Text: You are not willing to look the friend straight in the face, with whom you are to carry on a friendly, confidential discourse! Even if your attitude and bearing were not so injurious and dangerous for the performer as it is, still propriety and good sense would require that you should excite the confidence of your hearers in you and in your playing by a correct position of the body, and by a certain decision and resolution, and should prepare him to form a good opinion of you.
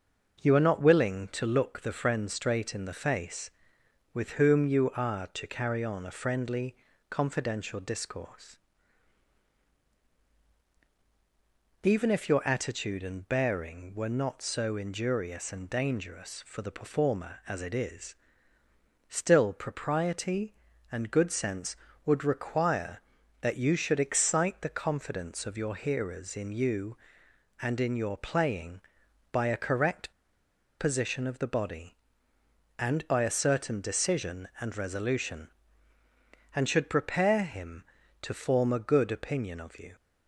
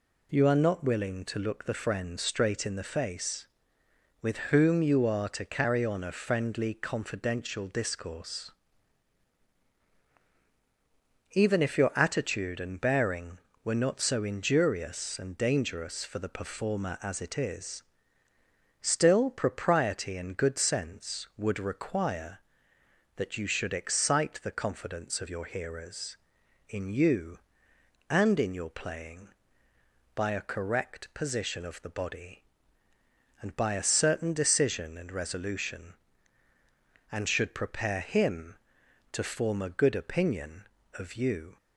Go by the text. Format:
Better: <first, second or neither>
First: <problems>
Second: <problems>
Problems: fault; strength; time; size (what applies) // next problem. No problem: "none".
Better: second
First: starts louder than the rest; noticeable; until 1.4 s; 6 dB // pauses between "correct" and "position"; noticeable; at 30.1 s; 0.68 s long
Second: none